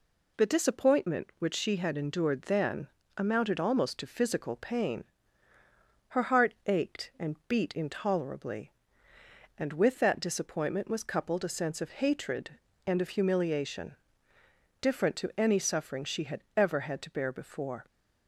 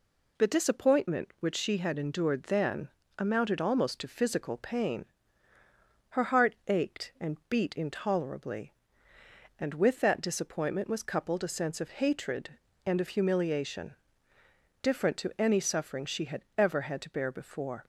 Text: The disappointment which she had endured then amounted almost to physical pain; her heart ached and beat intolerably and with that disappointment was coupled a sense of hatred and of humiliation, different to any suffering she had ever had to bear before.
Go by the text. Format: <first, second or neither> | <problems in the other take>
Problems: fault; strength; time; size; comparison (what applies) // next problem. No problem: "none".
neither | pauses between "then" and "amounted"; slight; the same in both